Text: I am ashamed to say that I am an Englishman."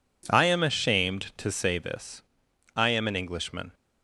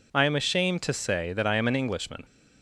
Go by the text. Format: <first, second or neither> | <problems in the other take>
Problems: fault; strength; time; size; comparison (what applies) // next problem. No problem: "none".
second | says "this" for "that"; at 1.7 s